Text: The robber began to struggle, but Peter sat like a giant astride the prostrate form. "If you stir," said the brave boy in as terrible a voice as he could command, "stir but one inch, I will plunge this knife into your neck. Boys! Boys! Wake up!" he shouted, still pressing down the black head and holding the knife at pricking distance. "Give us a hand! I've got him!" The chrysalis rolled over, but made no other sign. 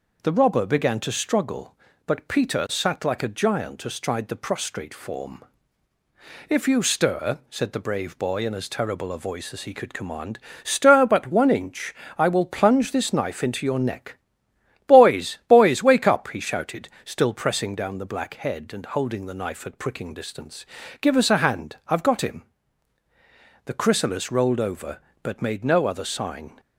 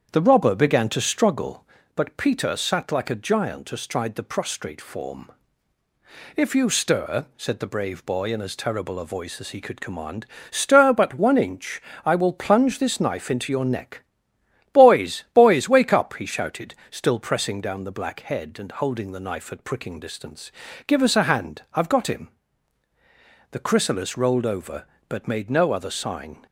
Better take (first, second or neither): first